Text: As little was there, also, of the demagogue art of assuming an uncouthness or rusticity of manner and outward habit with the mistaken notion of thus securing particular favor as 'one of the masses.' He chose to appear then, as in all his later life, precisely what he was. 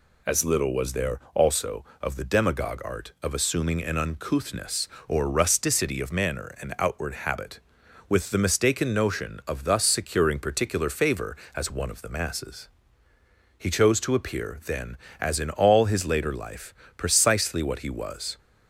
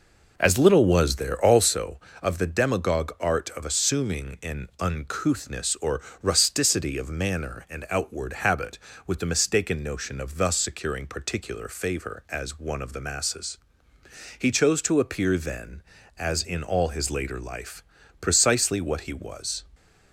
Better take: first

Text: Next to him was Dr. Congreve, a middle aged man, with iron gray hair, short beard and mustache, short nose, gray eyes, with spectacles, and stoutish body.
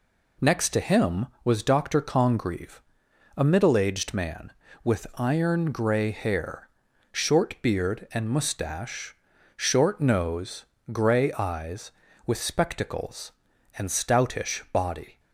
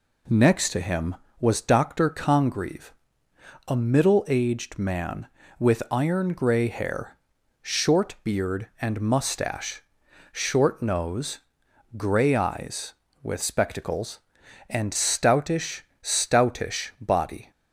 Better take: first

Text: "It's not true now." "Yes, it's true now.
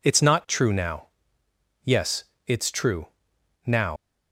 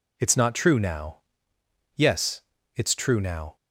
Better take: second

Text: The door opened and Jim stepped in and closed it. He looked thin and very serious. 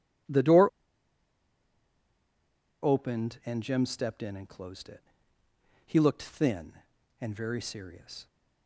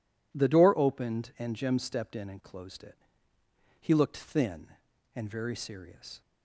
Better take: second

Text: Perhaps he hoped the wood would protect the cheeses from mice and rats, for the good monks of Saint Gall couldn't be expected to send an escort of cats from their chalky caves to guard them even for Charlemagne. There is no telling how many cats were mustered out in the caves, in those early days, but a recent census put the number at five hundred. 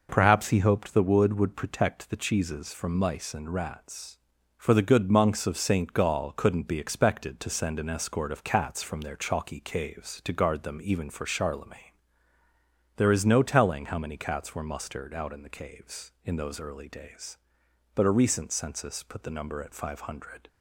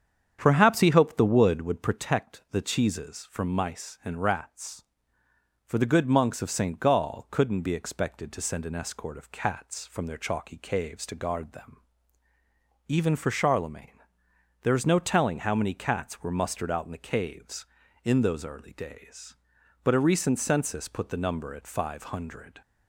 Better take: first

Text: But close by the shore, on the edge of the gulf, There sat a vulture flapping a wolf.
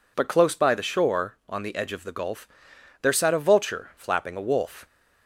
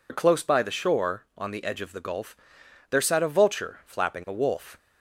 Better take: first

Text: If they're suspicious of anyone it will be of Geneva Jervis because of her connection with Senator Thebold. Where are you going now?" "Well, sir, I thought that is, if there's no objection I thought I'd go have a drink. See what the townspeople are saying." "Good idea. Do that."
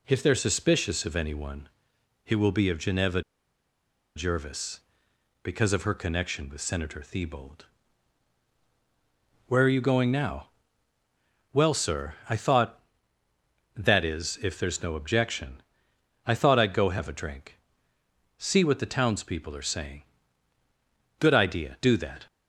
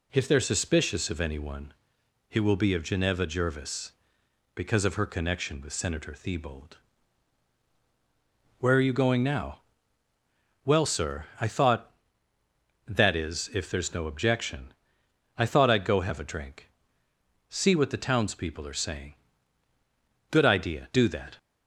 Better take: second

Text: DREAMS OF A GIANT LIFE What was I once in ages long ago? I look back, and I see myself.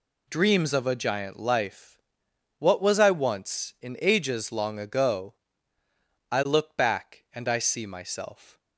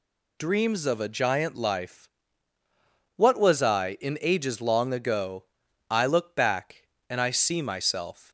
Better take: first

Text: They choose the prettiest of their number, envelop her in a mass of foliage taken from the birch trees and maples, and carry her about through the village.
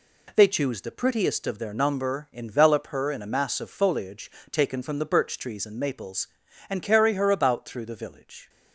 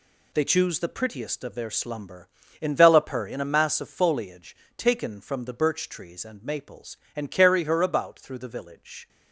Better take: first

